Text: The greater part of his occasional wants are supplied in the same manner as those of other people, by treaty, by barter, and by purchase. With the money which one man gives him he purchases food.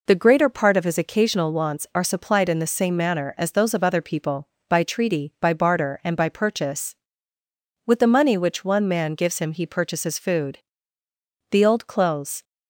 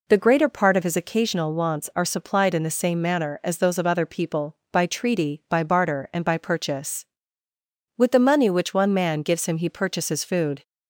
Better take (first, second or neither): second